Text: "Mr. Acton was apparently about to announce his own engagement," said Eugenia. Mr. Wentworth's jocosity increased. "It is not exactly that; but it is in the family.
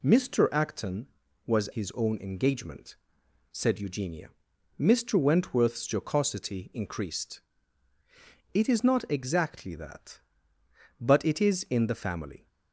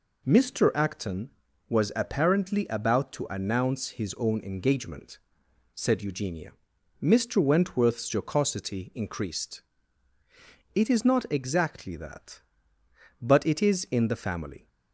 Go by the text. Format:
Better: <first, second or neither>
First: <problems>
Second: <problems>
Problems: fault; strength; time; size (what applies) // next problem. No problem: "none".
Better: second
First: skips "apparently about to announce"; at 1.6 s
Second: none